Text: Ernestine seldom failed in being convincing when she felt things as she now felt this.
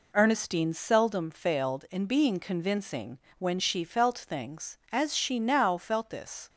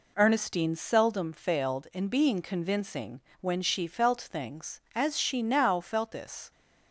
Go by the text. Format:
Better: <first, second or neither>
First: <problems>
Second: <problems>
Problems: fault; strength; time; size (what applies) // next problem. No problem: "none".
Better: neither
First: pauses between "convincing" and "when"; slight; at 3.1 s; 0.18 s long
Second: pauses between "convincing" and "when"; slight; at 3.2 s; 0.18 s long